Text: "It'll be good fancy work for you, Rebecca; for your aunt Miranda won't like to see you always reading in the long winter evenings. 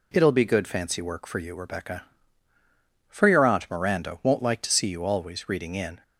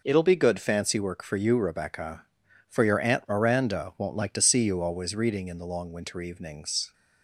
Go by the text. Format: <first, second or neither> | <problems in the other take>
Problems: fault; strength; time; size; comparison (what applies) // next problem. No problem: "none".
second | stops before "the long winter evenings"; at 6.0 s